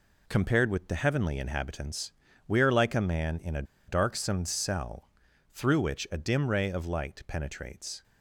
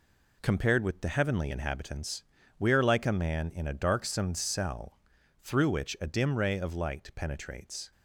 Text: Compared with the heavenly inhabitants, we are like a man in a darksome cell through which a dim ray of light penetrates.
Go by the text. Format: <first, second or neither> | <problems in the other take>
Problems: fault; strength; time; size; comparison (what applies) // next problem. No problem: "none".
second | pauses between "a" and "darksome"; slight; at 3.6 s; 0.25 s long // pauses between "cell" and "through"; at 5.0 s; 0.44 s long; also in the second